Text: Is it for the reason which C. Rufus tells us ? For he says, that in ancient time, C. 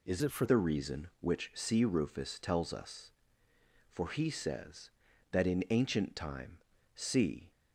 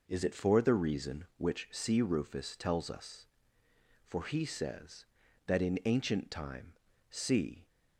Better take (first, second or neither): second